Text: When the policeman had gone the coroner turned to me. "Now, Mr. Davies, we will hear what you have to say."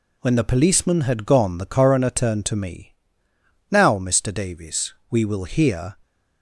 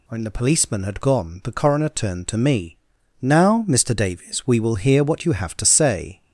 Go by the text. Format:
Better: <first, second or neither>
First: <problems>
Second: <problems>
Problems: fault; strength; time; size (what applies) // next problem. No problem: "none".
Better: second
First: stops before "what you have to say"; at 6.0 s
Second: none